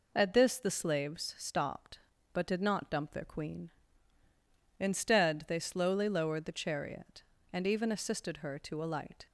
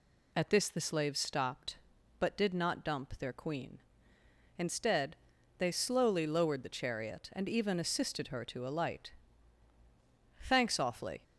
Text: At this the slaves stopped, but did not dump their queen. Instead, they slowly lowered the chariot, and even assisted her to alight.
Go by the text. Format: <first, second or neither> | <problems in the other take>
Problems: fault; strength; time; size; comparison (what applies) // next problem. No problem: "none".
first | goes on to say "Thanks awfully"; noticeable; from 10.4 s on; 0.82 s long